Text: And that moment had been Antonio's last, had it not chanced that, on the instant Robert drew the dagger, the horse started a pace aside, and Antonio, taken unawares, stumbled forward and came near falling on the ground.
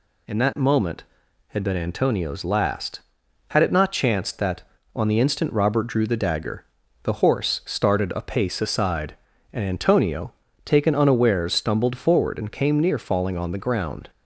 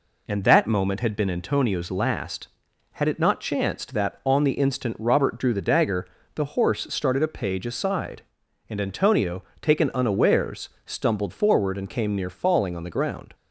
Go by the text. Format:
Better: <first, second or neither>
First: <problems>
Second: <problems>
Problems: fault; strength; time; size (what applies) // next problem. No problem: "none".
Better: first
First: none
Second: says "page" for "pace"; at 7.2 s